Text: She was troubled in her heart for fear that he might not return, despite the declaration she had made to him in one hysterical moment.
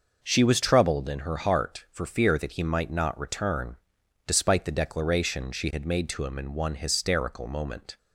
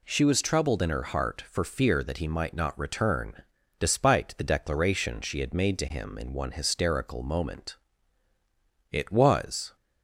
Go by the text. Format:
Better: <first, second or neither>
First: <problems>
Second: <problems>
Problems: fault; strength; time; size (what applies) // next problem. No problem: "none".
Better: first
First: none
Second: goes on to say "It was"; noticeable; from 8.9 s on; 0.84 s long